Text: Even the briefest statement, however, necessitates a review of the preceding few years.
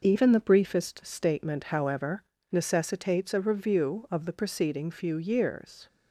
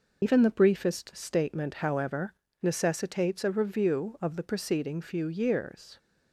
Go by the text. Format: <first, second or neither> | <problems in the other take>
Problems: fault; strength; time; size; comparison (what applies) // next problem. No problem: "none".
first | loses the start of "Even"; at 0.2 s; 95 ms